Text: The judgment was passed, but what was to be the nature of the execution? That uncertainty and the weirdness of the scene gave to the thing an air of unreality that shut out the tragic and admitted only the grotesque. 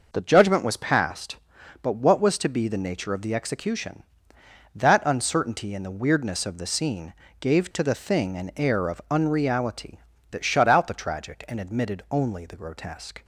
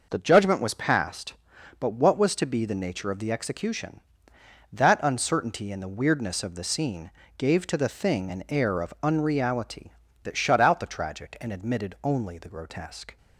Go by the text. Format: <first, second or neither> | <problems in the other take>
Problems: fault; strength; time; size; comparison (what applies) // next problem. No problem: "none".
neither | pauses between "scene" and "gave"; slight; the same in both